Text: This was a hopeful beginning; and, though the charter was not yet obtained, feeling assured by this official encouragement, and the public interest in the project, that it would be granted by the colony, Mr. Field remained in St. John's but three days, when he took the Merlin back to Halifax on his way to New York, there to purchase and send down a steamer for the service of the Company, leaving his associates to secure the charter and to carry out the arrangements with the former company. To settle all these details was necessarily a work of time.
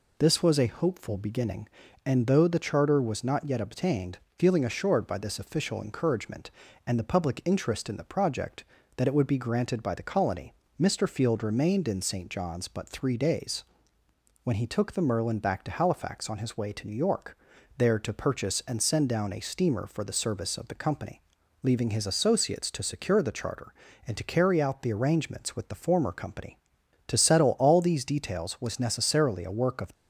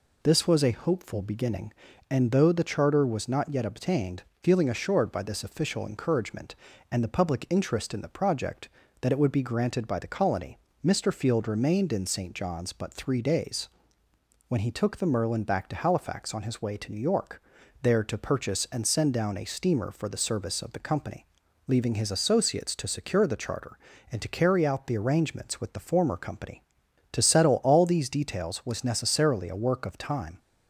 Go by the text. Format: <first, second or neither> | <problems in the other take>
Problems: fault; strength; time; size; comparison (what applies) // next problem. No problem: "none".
second | stops before "time"; at 29.9 s